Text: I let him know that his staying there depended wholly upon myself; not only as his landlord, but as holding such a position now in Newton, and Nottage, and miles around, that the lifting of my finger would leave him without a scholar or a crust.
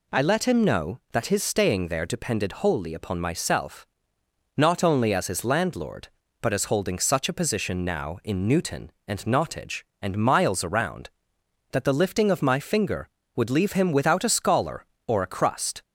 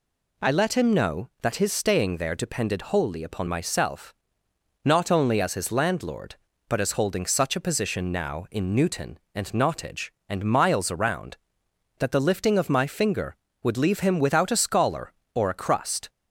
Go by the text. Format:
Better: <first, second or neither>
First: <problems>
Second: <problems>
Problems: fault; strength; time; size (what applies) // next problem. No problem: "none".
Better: neither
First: none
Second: none